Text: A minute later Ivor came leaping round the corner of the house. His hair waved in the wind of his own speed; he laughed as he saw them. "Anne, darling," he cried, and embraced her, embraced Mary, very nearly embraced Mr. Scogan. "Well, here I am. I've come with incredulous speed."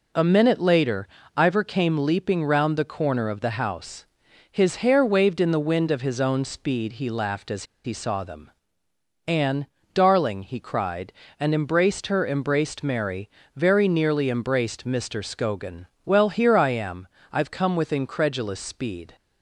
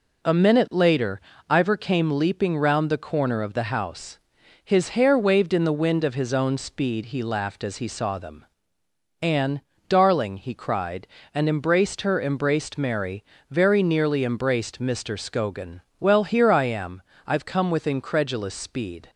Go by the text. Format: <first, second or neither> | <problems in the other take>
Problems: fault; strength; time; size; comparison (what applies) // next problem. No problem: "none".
second | pauses between "later" and "Ivor"; slight; at 1.0 s; 0.30 s long; slight in the second // pauses between "as" and "he"; slight; at 7.6 s; 0.20 s long